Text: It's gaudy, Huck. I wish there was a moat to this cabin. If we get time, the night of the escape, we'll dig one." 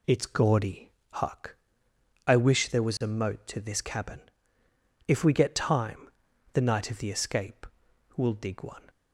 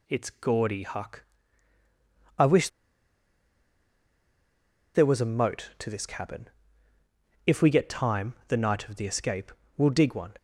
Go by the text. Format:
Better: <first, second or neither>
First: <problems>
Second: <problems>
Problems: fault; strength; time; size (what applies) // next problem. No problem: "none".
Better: first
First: none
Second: pauses between "wish" and "there"; strong; at 2.6 s; 2.2 s long